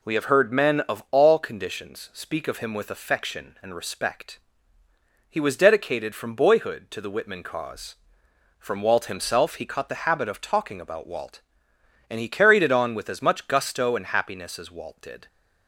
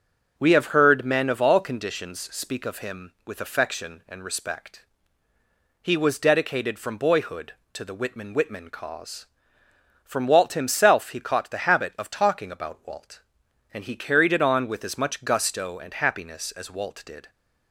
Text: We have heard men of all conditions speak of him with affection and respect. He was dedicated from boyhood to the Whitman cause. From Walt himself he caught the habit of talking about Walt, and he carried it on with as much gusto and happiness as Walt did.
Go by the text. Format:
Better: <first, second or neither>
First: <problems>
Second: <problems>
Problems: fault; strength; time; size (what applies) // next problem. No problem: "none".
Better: first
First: none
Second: starts louder than the rest; until 1.3 s; 6 dB // says "Whitman" twice; at 8.3 s